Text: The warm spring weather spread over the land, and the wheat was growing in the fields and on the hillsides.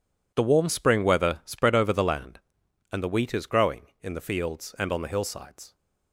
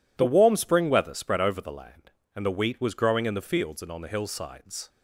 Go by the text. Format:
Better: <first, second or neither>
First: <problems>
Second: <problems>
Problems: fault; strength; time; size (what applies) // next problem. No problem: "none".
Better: second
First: says "is" for "was"; at 3.3 s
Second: none